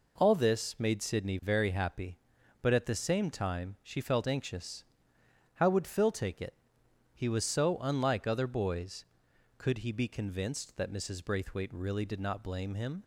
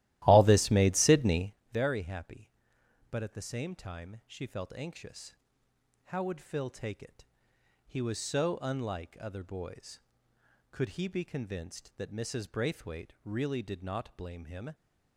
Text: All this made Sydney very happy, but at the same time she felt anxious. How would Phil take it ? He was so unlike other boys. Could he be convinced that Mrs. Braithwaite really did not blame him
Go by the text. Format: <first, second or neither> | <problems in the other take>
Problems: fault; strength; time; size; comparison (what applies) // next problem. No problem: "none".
first | starts louder than the rest; strong; until 1.6 s; 15.5 dB // pauses between "Sydney" and "very"; slight; at 1.5 s; 0.18 s long